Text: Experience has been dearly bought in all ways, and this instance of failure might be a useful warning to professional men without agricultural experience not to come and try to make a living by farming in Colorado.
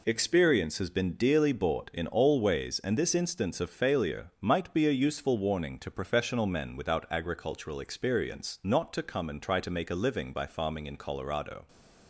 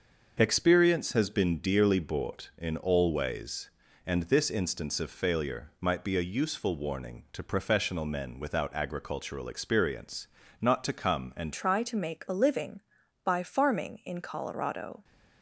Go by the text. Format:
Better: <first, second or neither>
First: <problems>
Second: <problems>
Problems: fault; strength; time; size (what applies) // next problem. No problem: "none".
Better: first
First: none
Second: starts louder than the rest; until 1.4 s; 6 dB // pauses between "experience" and "not"; slight; at 10.2 s; 0.32 s long // changes voice at "try"; from 11.5 s on; 3.5 s long